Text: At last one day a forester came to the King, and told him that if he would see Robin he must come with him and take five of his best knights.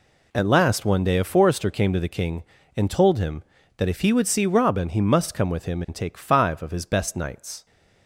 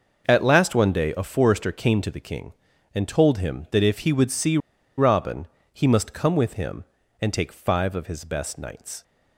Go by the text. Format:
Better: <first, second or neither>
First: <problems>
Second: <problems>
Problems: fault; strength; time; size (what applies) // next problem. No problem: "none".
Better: first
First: none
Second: pauses between "see" and "Robin"; at 4.5 s; 0.40 s long // pauses between "Robin" and "he"; slight; at 5.4 s; 0.26 s long